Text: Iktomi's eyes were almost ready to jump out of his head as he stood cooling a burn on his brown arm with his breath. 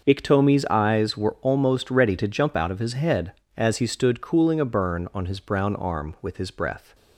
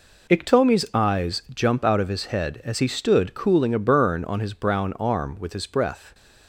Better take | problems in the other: first | skips "were almost ready to"; at 1.4 s // stays silent after the last word; slight; from 5.9 s on; 0.5 s long

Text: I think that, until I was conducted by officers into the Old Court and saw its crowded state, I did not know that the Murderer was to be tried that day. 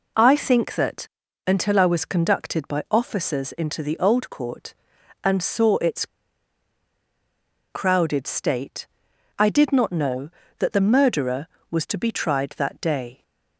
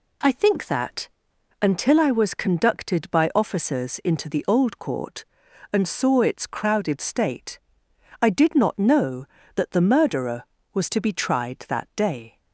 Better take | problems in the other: second | pauses between "its" and "crowded"; strong; at 6.0 s; 1.6 s long

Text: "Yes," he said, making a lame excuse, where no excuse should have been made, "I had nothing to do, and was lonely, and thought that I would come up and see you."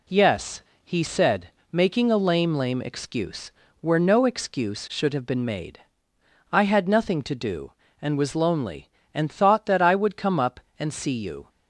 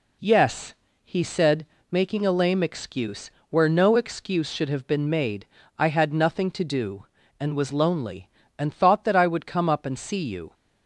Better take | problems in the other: second | says "lame" twice; at 2.5 s

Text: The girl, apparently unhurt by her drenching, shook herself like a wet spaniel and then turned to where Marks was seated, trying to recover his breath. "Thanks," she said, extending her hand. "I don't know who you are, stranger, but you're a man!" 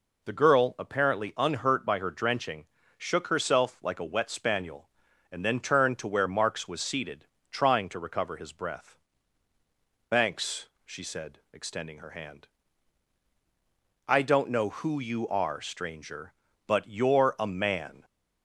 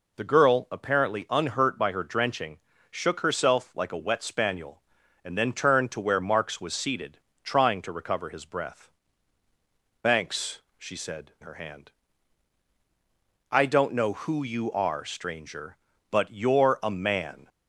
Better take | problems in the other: first | skips "extending"; at 11.3 s

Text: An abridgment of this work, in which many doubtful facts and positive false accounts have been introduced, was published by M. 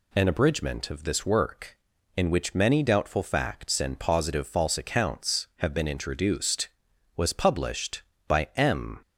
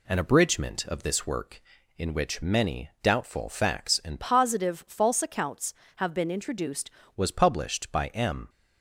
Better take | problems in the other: first | changes voice from "positive" to "introduced"; from 4.1 to 6.8 s; 2.7 s long

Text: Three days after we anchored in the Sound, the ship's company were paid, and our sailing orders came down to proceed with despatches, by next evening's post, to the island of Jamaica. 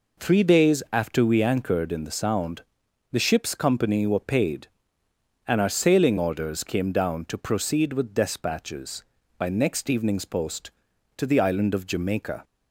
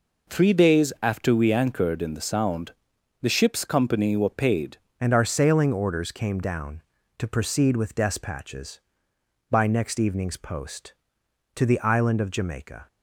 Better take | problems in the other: first | changes voice at "and"; from 4.9 s on; 7.9 s long

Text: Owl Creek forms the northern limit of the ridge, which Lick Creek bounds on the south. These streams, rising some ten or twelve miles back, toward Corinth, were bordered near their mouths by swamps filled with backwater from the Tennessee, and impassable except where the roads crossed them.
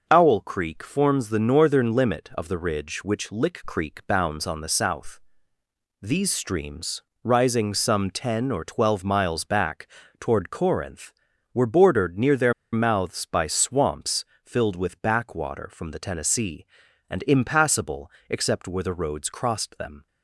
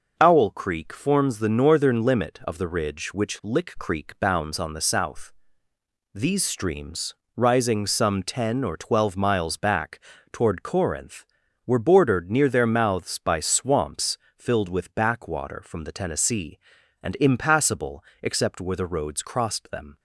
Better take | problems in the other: second | pauses between "their" and "mouths"; slight; at 12.5 s; 0.19 s long // pauses between "swamps" and "filled"; slight; at 14.2 s; 0.20 s long; slight in the second // pauses between "impassable" and "except"; slight; at 18.1 s; 0.18 s long; slight in the second

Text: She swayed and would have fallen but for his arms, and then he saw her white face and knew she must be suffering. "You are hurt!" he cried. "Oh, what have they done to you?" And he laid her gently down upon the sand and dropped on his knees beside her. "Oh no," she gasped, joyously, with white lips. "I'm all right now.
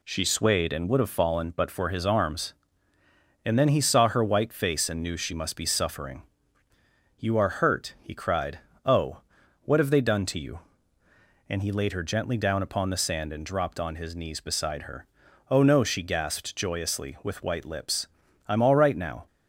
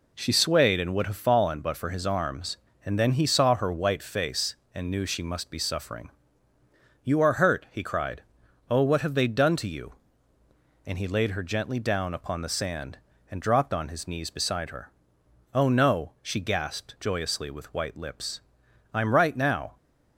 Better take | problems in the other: first | skips "all"; at 19.1 s

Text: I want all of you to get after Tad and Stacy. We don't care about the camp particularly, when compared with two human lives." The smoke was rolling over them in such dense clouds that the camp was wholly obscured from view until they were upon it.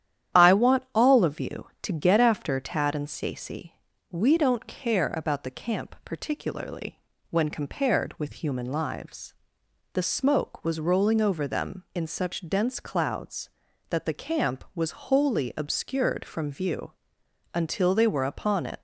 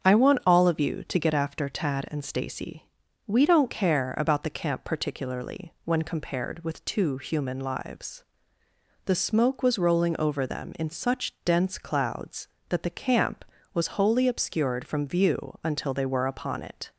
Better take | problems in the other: second | starts louder than the rest; strong; until 1.4 s; 10.5 dB; strong in the second // skips "two"; at 8.4 s // pauses between "view" and "until"; noticeable; at 16.9 s; 0.60 s long

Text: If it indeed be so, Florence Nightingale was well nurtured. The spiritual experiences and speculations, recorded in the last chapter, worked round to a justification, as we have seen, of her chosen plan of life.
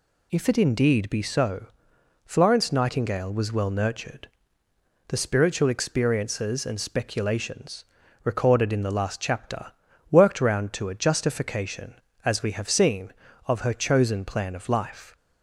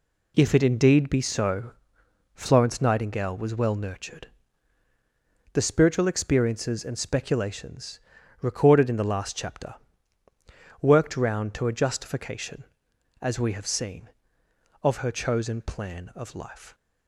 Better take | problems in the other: neither | none

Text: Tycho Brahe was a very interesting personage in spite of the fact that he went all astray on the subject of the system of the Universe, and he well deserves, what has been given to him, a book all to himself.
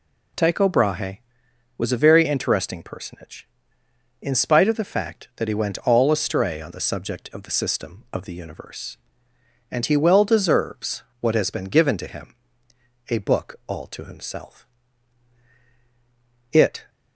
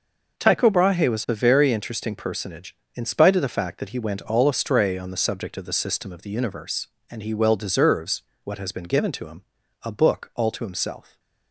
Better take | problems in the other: second | goes on to say "It"; slight; from 16.5 s on; 0.38 s long

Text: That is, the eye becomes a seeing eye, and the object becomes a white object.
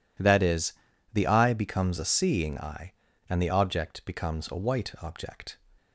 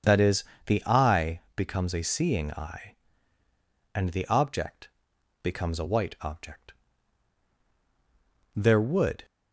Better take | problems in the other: first | starts louder than the rest; strong; until 1.2 s; 7 dB // pauses between "eye" and "becomes"; slight; at 1.4 s; 0.16 s long // pauses between "object" and "becomes"; noticeable; at 4.8 s; 0.52 s long // goes on to say "There would"; noticeable; from 8.5 s on; 0.70 s long

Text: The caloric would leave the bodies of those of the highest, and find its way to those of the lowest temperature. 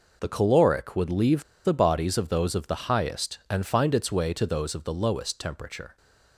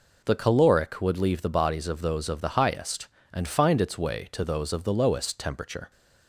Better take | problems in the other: second | pauses between "leave" and "the"; slight; at 1.4 s; 0.21 s long

